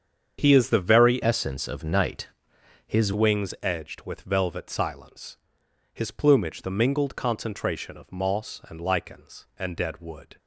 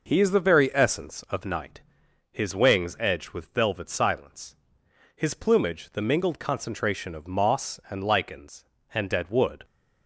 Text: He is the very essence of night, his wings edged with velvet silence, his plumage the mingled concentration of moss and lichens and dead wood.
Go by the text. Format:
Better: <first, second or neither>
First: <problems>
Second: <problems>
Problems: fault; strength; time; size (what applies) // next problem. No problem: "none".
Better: second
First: starts louder than the rest; strong; until 1.4 s; 7.5 dB // changes voice from "essence" to "his"; from 1.2 to 3.1 s; 1.9 s long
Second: none